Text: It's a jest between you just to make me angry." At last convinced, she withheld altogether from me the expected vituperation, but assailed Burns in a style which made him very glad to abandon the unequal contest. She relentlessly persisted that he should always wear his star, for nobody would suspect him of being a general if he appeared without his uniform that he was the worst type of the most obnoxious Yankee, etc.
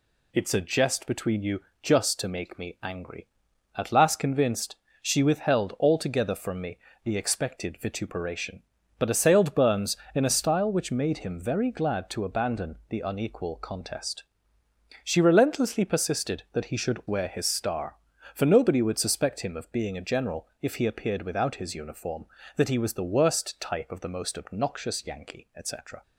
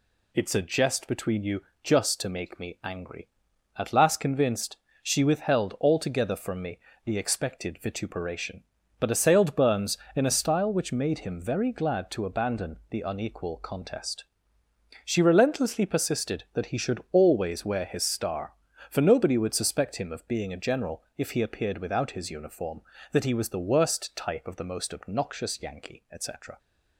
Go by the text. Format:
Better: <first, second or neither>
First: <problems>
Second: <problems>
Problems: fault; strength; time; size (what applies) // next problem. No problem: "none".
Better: second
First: pauses between "you" and "just"; slight; at 1.6 s; 0.22 s long // pauses between "me" and "the"; slight; at 6.7 s; 0.26 s long // skips "always"; at 17.0 s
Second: pauses between "you" and "just"; slight; at 1.6 s; 0.22 s long // pauses between "me" and "the"; slight; at 6.7 s; 0.26 s long